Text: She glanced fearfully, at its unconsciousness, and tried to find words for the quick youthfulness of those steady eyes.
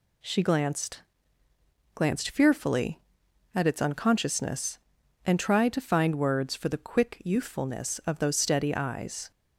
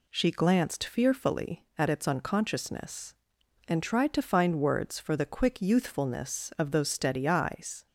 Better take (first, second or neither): second